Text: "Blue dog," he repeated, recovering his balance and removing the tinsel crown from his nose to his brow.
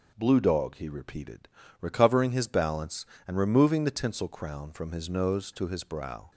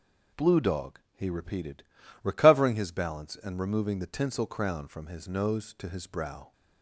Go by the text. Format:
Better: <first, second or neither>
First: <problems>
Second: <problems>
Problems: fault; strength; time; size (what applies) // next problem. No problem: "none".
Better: neither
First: none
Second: none